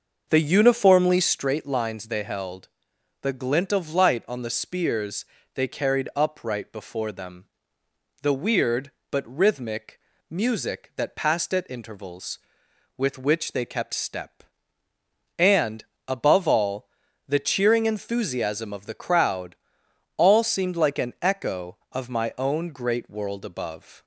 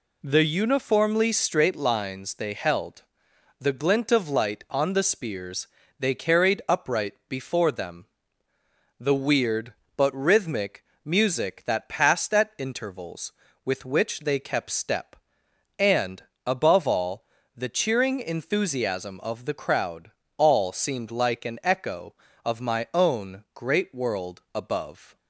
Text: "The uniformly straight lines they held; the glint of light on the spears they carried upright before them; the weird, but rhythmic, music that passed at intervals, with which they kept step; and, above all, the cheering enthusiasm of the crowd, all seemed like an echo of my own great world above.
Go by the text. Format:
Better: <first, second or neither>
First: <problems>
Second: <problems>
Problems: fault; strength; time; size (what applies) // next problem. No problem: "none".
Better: second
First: starts louder than the rest; until 1.4 s; 6 dB // pauses between "spears" and "they"; slight; at 5.2 s; 0.30 s long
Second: pauses between "spears" and "they"; slight; at 5.6 s; 0.32 s long